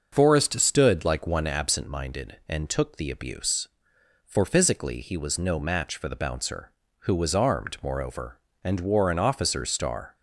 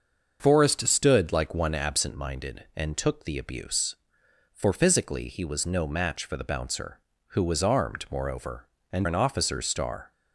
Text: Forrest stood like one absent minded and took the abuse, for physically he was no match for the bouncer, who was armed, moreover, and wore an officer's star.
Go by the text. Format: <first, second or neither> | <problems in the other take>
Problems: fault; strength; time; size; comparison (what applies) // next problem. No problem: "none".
first | starts louder than the rest; until 1.4 s; 6.5 dB; also in the first // skips "wore"; at 9.0 s